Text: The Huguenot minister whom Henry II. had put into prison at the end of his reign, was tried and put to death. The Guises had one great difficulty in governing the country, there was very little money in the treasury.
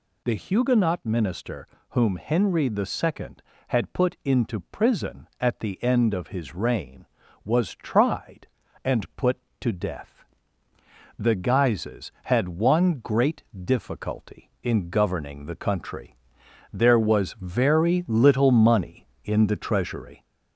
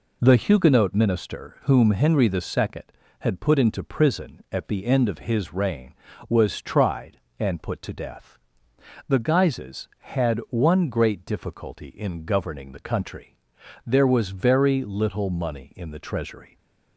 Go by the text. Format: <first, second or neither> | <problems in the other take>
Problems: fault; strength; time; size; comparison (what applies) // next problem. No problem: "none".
second | gets louder; slight; throughout; 3 dB // pauses between "minister" and "whom"; slight; at 1.6 s; 0.22 s long // pauses between "great" and "difficulty"; slight; at 13.4 s; 0.22 s long